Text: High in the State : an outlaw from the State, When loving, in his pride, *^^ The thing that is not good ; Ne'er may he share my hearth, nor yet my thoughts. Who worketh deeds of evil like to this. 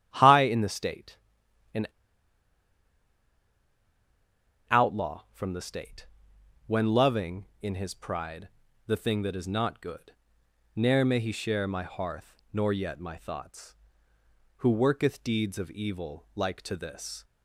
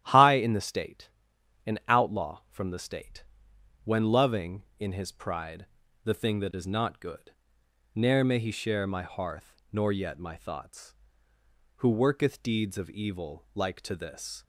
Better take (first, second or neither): second